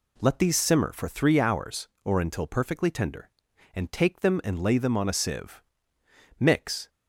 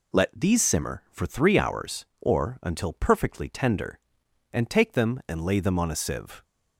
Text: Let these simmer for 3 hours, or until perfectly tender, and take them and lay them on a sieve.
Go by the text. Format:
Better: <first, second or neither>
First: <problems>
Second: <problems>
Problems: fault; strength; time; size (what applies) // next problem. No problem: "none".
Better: second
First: goes on to say "Mix"; from 6.3 s on; 0.50 s long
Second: none